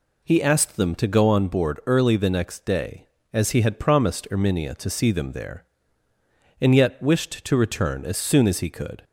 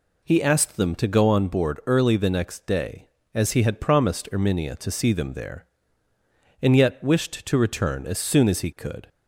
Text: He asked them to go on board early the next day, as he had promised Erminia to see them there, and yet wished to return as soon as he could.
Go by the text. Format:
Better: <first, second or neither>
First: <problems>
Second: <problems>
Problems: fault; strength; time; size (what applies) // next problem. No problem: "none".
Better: neither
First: none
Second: none